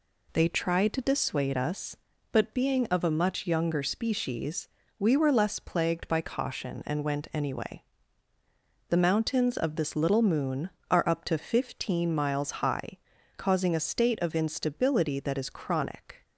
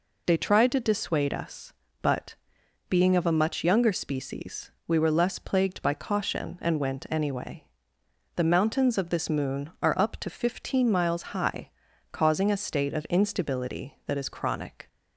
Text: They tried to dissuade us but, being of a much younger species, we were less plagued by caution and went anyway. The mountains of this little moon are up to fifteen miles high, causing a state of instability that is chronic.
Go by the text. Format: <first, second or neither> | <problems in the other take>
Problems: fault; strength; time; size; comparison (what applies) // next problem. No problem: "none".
first | skips "little"; at 9.2 s